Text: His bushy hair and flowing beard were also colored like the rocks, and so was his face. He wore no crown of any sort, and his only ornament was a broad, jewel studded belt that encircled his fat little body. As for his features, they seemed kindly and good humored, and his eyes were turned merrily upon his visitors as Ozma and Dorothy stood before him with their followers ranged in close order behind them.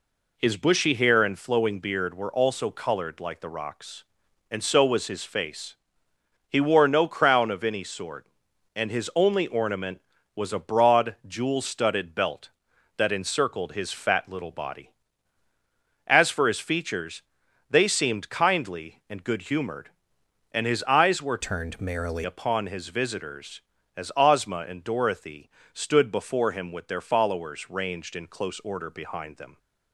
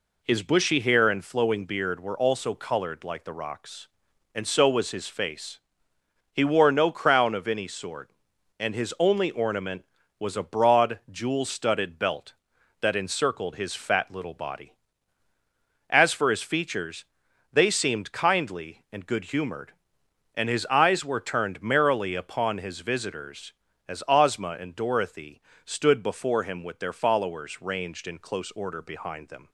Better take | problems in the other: second | changes voice from "turned" to "merrily"; from 21.4 to 22.2 s; 0.8 s long // pauses between "Dorothy" and "stood"; slight; at 25.4 s; 0.24 s long; slight in the second

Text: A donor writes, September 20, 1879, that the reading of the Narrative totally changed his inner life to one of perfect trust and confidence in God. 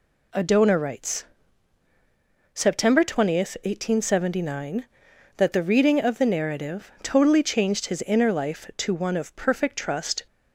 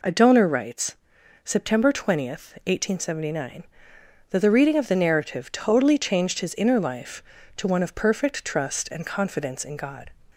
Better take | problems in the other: second | stops before "and confidence in God"; at 10.2 s

